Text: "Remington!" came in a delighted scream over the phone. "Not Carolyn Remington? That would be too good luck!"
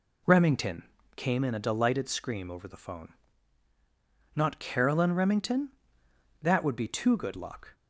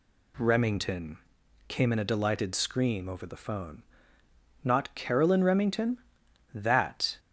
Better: first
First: none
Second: stops before "would be too good luck"; at 7.1 s

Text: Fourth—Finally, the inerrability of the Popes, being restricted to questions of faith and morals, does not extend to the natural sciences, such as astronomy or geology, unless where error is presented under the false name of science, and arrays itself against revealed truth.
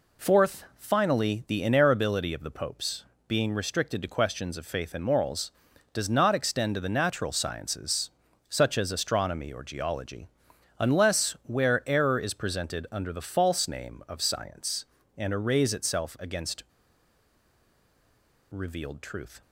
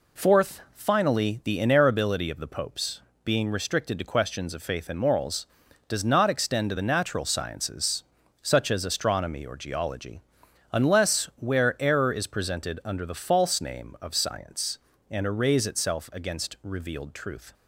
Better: second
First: pauses between "against" and "revealed"; strong; at 16.6 s; 1.8 s long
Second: none

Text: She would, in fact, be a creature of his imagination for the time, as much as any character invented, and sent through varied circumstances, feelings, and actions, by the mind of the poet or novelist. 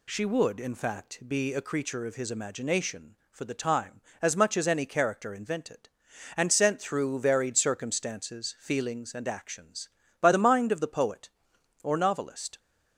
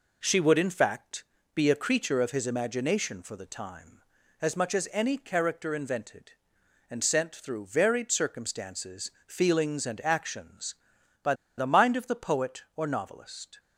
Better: first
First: none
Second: pauses between "by" and "the"; slight; at 11.3 s; 0.23 s long

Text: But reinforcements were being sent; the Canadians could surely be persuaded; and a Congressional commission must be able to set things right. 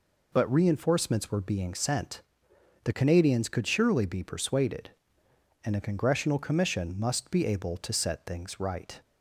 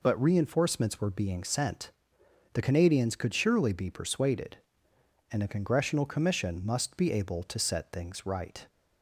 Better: neither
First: none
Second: none

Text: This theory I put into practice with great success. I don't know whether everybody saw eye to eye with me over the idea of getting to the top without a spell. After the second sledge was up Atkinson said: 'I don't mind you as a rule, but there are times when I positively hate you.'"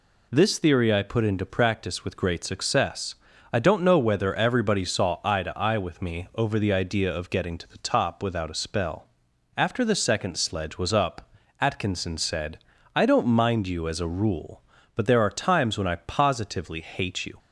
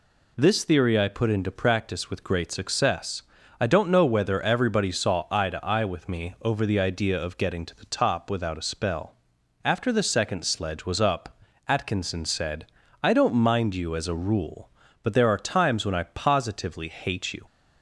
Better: neither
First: pauses between "up" and "Atkinson"; slight; at 11.3 s; 0.28 s long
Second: pauses between "up" and "Atkinson"; slight; at 11.3 s; 0.28 s long

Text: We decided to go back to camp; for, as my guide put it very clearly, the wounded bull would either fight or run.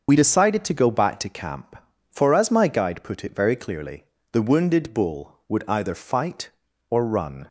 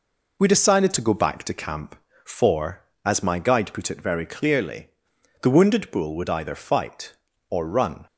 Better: second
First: loses the start of "We"; at 0.0 s; 45 ms // starts louder than the rest; until 1.0 s; 6 dB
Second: none

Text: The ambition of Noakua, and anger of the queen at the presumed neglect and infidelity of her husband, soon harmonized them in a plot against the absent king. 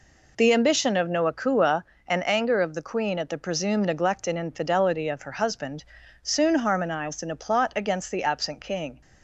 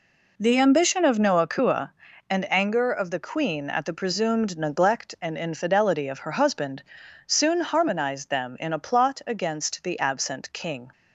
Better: second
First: skips "them"; at 7.2 s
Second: none

